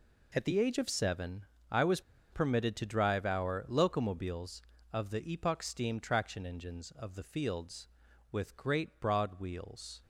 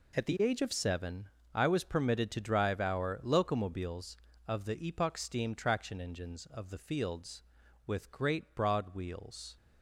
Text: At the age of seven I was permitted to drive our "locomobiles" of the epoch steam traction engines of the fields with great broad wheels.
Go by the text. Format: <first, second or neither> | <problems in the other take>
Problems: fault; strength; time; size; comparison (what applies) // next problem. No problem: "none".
second | pauses between "seven" and "I"; slight; at 1.4 s; 0.26 s long; slight in the second // pauses between "was" and "permitted"; slight; at 2.0 s; 0.30 s long